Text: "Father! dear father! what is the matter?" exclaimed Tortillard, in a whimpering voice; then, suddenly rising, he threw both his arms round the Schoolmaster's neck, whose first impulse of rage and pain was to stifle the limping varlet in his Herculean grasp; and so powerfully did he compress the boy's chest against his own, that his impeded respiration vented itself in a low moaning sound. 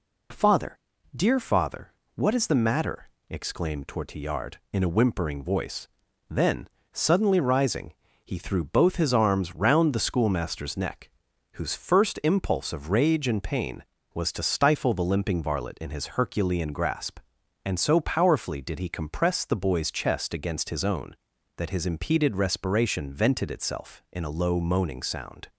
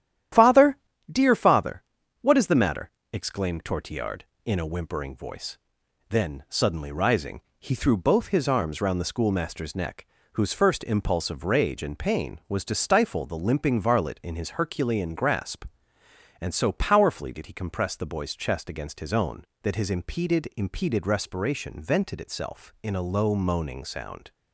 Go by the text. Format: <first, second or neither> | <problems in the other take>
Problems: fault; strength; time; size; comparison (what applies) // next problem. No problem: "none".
first | starts louder than the rest; strong; until 1.6 s; 11 dB // says "impeded" twice; at 20.5 s